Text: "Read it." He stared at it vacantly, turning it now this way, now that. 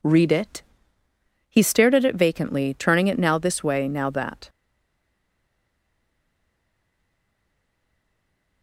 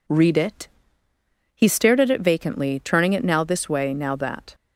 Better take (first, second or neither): second